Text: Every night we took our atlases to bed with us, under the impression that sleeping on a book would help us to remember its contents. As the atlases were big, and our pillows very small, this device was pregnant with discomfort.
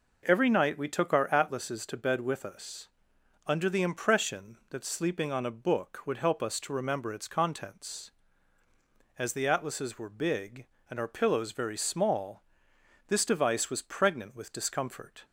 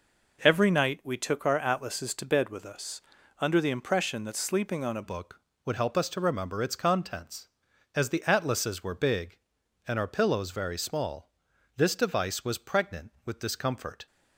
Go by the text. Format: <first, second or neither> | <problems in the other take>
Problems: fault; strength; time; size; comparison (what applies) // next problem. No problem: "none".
first | changes voice at "book"; from 5.0 s on; 9.0 s long